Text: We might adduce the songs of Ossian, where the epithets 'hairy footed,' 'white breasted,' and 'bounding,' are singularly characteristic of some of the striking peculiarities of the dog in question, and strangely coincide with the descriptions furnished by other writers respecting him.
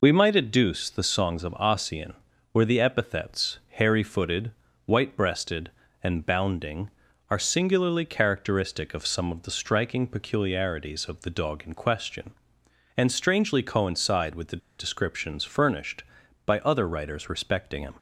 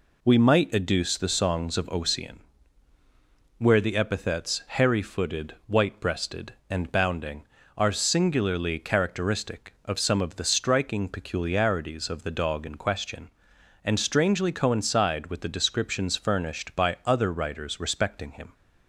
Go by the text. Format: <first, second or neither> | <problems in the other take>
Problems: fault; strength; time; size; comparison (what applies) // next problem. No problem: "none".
second | pauses between "the" and "descriptions"; slight; at 14.6 s; 0.20 s long